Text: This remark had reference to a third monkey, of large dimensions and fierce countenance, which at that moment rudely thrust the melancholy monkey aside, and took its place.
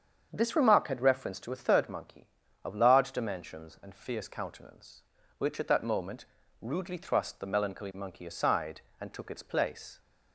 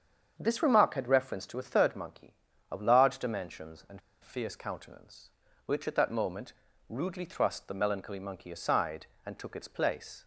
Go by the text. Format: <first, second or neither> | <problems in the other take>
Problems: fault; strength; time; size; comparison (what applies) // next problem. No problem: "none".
first | starts louder than the rest; strong; until 1.4 s; 7 dB; strong in the first // pauses between "and" and "fierce"; slight; at 3.9 s; 0.22 s long // pauses between "moment" and "rudely"; slight; at 6.5 s; 0.36 s long; slight in the first